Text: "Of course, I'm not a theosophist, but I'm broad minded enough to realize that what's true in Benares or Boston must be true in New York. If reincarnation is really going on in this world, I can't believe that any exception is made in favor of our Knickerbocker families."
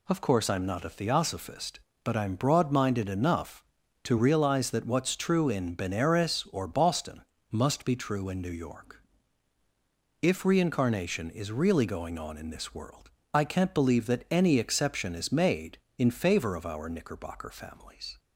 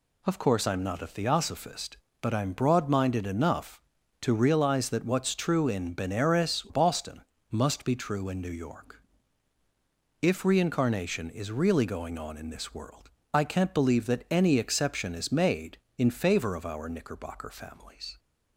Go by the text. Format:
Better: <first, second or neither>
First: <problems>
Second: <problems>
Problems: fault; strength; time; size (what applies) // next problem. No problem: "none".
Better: first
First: pauses between "Boston" and "must"; slight; at 7.2 s; 0.30 s long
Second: skips "or"; at 6.6 s // pauses between "Boston" and "must"; slight; at 7.2 s; 0.30 s long